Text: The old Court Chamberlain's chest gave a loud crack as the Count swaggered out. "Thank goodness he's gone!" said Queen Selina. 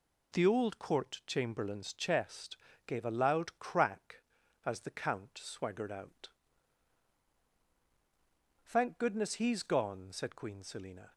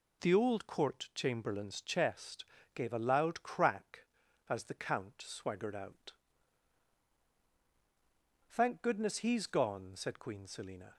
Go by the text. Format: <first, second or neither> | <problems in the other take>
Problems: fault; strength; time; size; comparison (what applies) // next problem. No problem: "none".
neither | pauses between "chest" and "gave"; slight; the same in both